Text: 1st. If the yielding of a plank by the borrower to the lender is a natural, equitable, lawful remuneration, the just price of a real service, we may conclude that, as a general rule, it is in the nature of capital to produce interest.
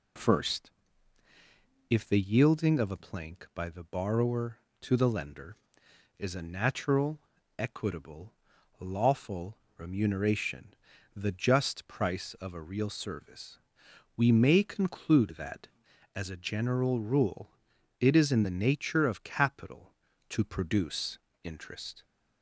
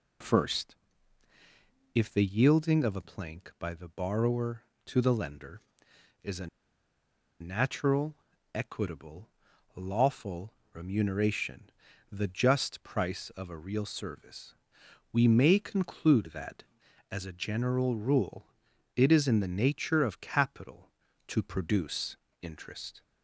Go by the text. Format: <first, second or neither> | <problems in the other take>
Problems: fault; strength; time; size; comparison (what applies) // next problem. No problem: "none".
first | pauses between "a" and "natural"; noticeable; at 6.4 s; 0.92 s long // pauses between "lawful" and "remuneration"; slight; at 10.5 s; 0.20 s long; slight in the first // pauses between "produce" and "interest"; slight; at 22.1 s; 0.24 s long; slight in the first